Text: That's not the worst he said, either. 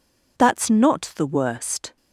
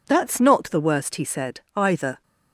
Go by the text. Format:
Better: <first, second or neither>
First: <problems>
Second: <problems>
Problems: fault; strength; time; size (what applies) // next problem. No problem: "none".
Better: second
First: stops before "he said either"; at 1.9 s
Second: none